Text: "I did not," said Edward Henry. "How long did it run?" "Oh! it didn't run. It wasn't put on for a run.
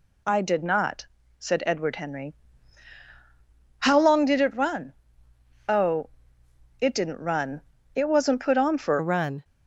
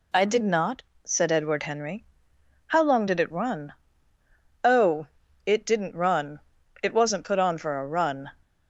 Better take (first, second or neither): second